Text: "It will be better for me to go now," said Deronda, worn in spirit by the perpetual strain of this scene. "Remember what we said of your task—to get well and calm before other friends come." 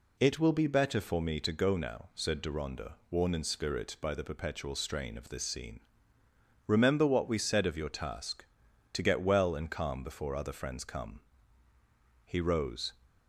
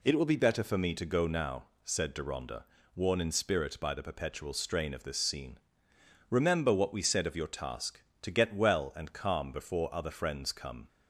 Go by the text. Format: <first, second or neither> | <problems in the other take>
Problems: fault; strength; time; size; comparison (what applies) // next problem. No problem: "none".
second | goes on to say "He rose"; noticeable; from 12.2 s on; 0.68 s long